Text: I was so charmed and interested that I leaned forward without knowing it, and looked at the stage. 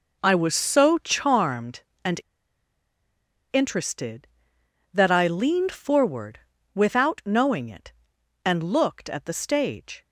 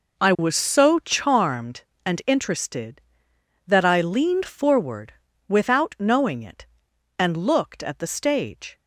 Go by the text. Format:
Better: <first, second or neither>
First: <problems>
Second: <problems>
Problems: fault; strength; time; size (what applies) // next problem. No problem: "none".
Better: second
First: pauses between "and" and "interested"; strong; at 2.1 s; 1.3 s long // pauses between "forward" and "without"; slight; at 6.4 s; 0.34 s long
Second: pauses between "forward" and "without"; slight; at 5.1 s; 0.34 s long